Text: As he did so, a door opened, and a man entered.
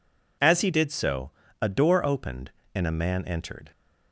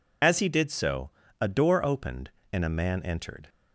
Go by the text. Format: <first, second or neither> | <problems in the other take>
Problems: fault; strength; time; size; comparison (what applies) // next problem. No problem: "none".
first | loses the start of "As"; at 0.2 s; 40 ms